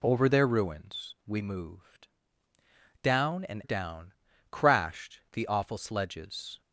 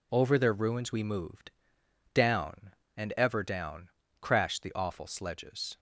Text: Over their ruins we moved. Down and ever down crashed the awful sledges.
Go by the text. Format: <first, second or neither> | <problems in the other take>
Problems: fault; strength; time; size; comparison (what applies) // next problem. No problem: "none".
second | skips "ever"; at 3.6 s // pauses between "down" and "crashed"; slight; at 4.1 s; 0.36 s long; slight in the second